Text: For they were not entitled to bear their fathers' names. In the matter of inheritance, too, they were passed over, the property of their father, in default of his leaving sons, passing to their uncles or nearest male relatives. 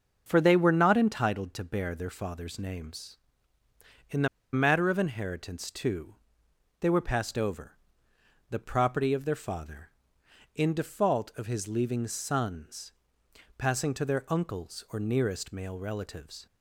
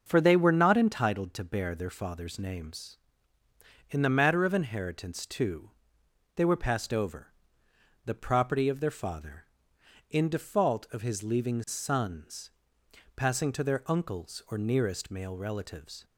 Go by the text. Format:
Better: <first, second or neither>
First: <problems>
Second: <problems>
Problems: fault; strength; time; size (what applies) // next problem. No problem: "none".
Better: second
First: starts louder than the rest; until 1.2 s; 6.5 dB // pauses between "the" and "matter"; slight; at 4.2 s; 0.25 s long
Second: starts louder than the rest; until 1.0 s; 6.5 dB